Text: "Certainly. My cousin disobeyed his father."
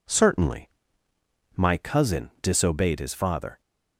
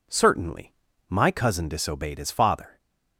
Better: neither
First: none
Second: none

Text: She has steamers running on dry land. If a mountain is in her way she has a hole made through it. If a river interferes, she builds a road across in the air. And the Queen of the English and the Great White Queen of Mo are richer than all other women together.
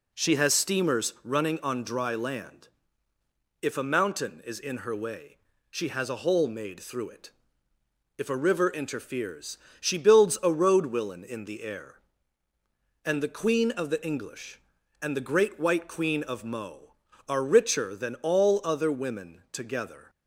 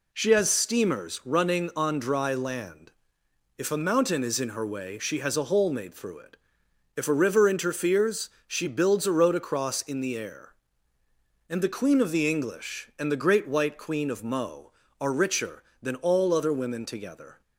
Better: second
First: pauses between "way" and "she"; slight; at 5.3 s; 0.36 s long // says "willen" for "across"; at 10.8 s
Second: none

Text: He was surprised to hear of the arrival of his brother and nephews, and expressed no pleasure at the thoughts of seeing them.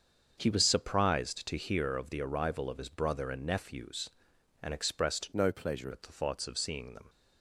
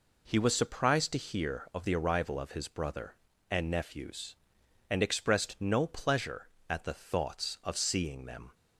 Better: second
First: starts louder than the rest; until 1.4 s; 6.5 dB // changes voice from "no" to "pleasure"; from 5.3 to 5.8 s; 0.5 s long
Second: none

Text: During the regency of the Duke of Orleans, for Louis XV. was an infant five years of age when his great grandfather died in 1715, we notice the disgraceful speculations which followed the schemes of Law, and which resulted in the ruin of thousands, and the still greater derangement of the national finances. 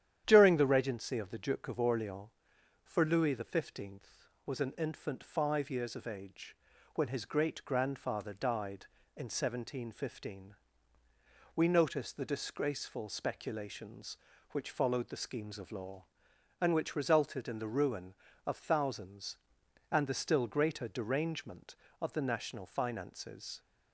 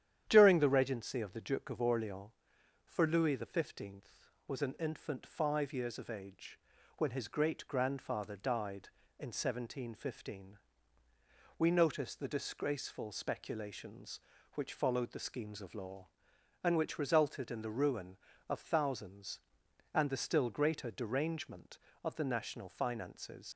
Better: first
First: starts louder than the rest; strong; until 1.2 s; 10 dB // pauses between "age" and "when"; at 6.5 s; 0.40 s long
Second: starts louder than the rest; strong; until 1.3 s; 10 dB // pauses between "age" and "when"; at 6.5 s; 0.40 s long // leaves "finances" unfinished; at 23.5 s; 100 ms

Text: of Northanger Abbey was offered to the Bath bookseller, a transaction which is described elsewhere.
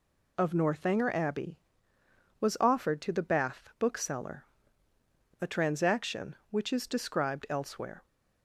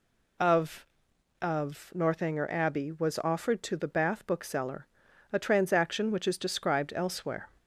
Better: first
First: none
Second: says "of" twice; at 1.3 s

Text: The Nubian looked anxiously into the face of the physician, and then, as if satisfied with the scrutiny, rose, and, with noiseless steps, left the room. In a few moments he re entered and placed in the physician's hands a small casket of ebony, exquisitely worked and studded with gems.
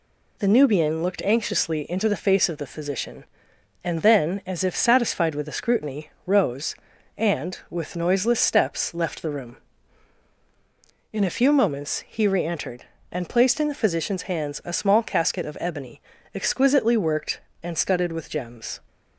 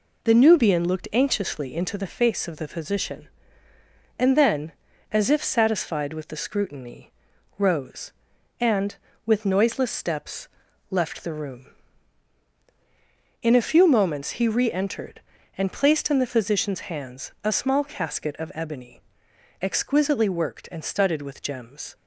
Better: neither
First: none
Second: none

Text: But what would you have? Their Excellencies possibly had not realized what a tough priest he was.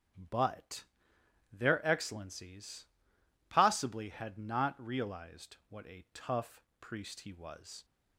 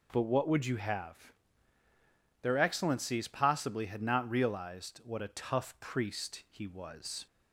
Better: second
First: starts louder than the rest; until 1.8 s; 7 dB // skips "what would you have"; at 1.1 s // pauses between "Excellencies" and "possibly"; noticeable; at 2.8 s; 0.64 s long // pauses between "tough" and "priest"; slight; at 6.6 s; 0.18 s long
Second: none

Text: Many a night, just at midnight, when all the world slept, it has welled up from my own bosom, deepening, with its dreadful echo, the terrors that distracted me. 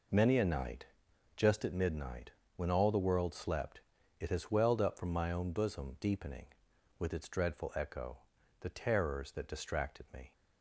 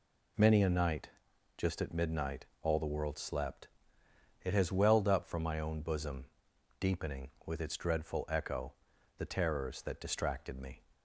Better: first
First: none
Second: skips "when"; at 2.5 s

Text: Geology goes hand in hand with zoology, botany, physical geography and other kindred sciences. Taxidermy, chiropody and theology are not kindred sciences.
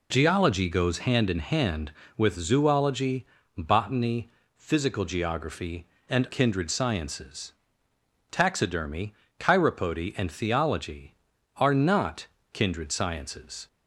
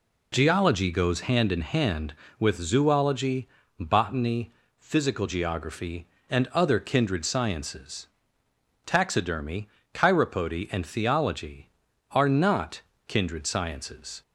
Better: second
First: skips "other"; at 6.2 s // pauses between "not" and "kindred"; slight; at 12.2 s; 0.28 s long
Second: pauses between "not" and "kindred"; slight; at 12.7 s; 0.28 s long

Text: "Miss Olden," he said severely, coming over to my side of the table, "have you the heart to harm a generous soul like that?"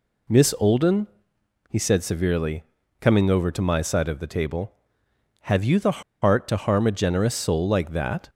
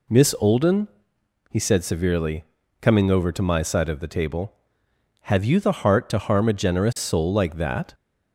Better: second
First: pauses between "the" and "heart"; slight; at 6.0 s; 0.19 s long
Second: none

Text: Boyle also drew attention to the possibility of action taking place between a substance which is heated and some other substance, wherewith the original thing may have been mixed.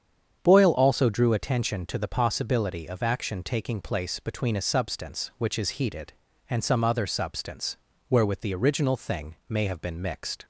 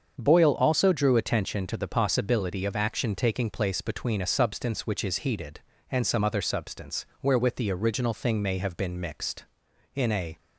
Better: first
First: starts louder than the rest; strong; until 1.4 s; 8 dB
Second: starts louder than the rest; until 1.1 s; 7 dB // goes on to say "In a"; slight; from 9.9 s on; 0.44 s long

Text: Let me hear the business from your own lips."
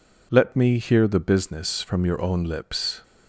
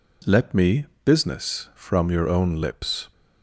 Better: first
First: none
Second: skips "hear the"; at 0.9 s

